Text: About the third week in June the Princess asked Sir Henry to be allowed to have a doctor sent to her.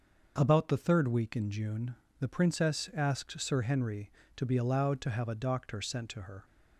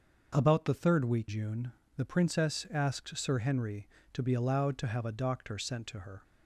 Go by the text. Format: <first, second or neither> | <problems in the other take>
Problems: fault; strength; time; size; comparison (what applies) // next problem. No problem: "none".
first | starts louder than the rest; until 1.3 s; 6 dB; also in the first // skips "in"; at 1.2 s // pauses between "June" and "the"; slight; at 1.7 s; 0.24 s long; slight in the first